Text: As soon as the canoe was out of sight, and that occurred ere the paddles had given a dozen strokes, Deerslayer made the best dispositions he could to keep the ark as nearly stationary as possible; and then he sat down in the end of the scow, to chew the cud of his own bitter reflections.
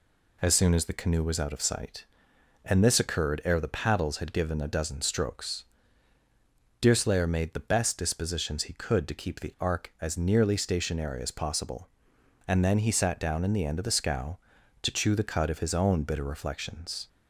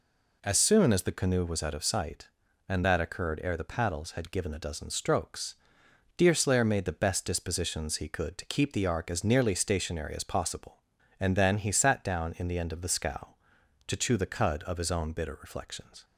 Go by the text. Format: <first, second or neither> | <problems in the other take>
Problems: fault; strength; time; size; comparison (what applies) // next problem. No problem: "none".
second | says "this" for "that"; at 2.8 s